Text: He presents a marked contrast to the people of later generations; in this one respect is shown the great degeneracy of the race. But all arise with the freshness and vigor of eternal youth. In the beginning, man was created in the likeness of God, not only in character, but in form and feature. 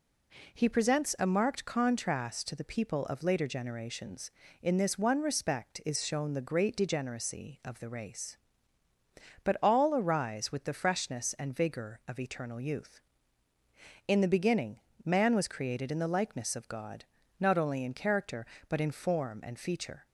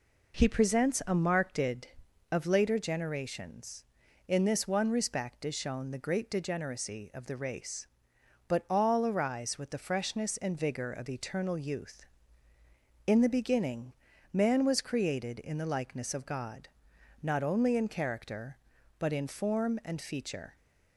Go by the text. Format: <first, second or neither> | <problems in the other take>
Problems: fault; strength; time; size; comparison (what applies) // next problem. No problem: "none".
first | skips "contrast to the people"; at 1.9 s